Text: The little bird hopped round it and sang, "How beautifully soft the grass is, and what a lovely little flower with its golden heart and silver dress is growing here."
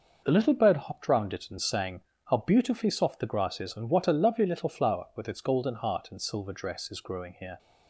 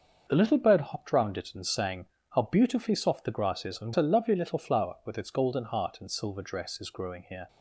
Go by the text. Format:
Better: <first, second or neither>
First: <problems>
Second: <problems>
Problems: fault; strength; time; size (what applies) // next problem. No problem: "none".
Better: first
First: none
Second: starts louder than the rest; until 1.2 s; 6.5 dB // skips "what"; at 3.9 s